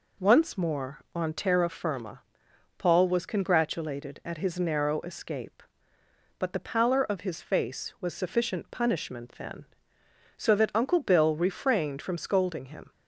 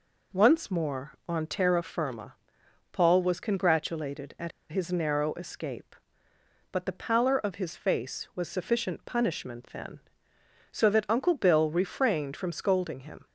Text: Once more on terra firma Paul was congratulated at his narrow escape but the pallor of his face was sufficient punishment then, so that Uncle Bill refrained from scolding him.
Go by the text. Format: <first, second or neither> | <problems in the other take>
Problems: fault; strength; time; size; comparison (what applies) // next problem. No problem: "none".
first | pauses between "firma" and "Paul"; noticeable; at 2.3 s; 0.60 s long; noticeable in the first // pauses between "at" and "his"; slight; at 4.5 s; 0.20 s long